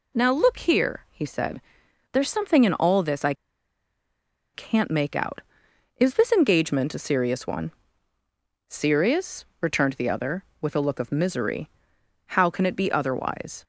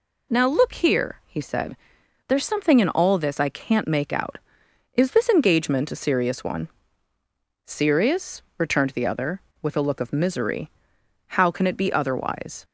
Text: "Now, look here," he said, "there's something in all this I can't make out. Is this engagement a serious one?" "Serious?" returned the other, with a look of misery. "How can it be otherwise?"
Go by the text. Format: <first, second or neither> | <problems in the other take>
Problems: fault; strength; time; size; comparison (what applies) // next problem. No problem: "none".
second | pauses between "I" and "can't"; at 3.3 s; 1.2 s long